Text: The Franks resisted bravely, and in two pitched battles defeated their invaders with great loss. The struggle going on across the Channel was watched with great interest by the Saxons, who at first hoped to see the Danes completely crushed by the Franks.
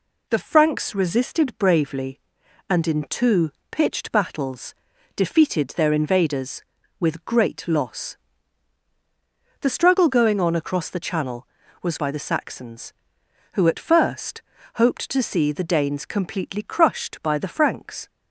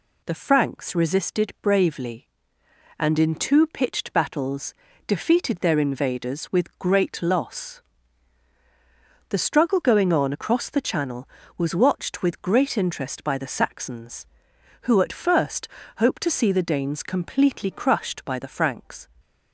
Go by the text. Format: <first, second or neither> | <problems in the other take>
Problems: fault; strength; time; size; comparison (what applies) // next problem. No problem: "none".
second | pauses between "two" and "pitched"; slight; at 3.5 s; 0.20 s long // pauses between "battles" and "defeated"; at 4.7 s; 0.40 s long; slight in the second // skips "watched with great interest"; at 11.9 s // pauses between "first" and "hoped"; slight; at 14.4 s; 0.32 s long; slight in the second